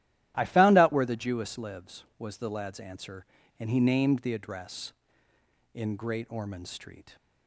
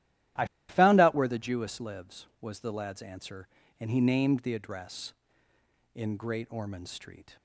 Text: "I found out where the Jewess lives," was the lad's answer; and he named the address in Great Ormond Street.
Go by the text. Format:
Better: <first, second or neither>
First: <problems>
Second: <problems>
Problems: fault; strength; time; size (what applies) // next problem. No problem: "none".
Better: first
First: starts louder than the rest; strong; until 1.3 s; 13 dB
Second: starts louder than the rest; strong; until 1.6 s; 13.5 dB // pauses between "I" and "found"; slight; at 0.4 s; 0.24 s long